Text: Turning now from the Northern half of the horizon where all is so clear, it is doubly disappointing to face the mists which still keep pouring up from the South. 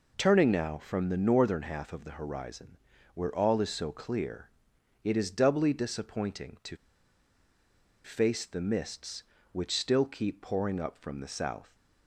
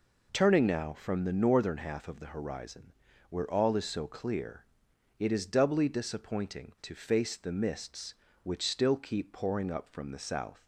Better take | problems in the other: second | pauses between "horizon" and "where"; at 2.7 s; 0.38 s long; also in the second // pauses between "to" and "face"; strong; at 6.7 s; 1.2 s long

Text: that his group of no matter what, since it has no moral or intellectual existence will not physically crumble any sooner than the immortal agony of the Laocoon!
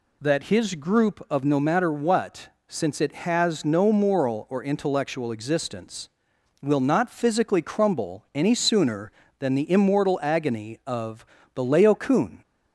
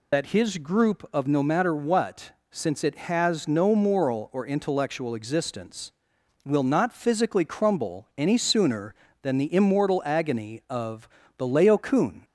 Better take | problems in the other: first | loses the start of "that"; at 0.1 s; 85 ms // pauses between "of" and "the"; slight; at 11.0 s; 0.30 s long; slight in the first

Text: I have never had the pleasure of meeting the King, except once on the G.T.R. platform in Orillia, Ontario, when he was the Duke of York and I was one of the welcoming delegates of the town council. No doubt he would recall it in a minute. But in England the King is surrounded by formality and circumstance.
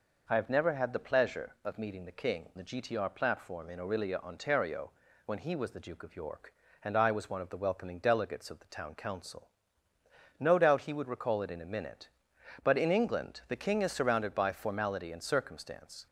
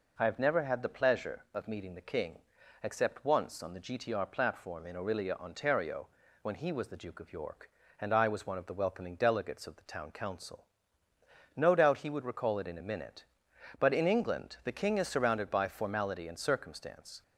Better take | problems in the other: second | skips "except once on"; at 2.5 s

